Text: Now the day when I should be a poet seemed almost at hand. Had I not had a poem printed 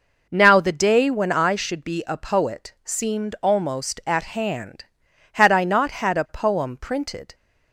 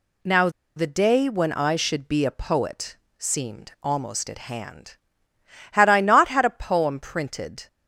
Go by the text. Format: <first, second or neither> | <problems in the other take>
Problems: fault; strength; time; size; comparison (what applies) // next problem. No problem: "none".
first | pauses between "Now" and "the"; slight; at 0.4 s; 0.27 s long // pauses between "poet" and "seemed"; slight; at 2.9 s; 0.20 s long